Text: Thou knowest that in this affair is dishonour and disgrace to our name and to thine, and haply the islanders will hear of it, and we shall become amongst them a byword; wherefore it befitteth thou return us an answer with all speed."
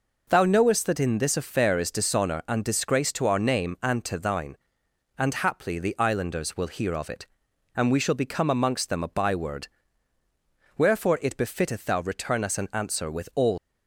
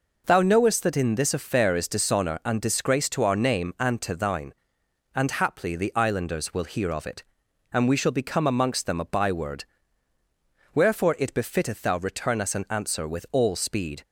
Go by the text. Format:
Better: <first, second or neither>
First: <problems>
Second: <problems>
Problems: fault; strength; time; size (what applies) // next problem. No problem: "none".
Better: second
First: stops before "speed"; at 13.5 s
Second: none